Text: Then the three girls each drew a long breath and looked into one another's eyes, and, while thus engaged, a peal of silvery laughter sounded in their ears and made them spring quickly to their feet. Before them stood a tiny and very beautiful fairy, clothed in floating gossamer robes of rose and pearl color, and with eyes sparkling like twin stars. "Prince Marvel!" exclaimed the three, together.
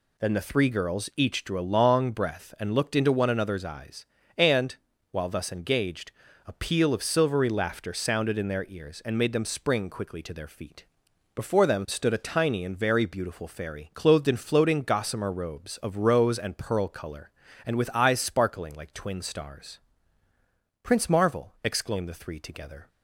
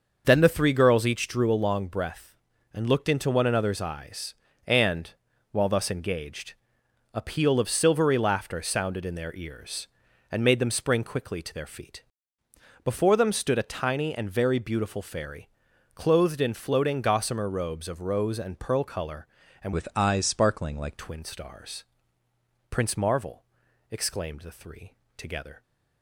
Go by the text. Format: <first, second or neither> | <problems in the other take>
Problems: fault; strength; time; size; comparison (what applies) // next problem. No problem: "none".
first | starts louder than the rest; until 1.2 s; 6 dB // changes voice from "with" to "like"; from 19.7 to 20.9 s; 1.2 s long